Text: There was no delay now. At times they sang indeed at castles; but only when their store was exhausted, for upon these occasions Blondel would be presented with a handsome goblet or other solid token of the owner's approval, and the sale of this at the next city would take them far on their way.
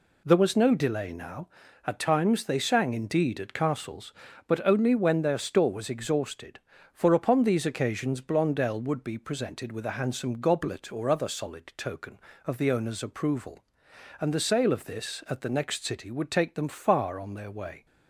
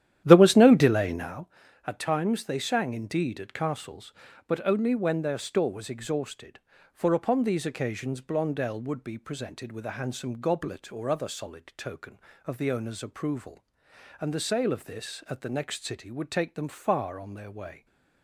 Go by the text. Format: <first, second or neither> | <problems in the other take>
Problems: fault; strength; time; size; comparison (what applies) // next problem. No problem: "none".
first | starts louder than the rest; strong; until 1.4 s; 11.5 dB // stays silent after the last word; slight; from 17.7 s on; 0.5 s long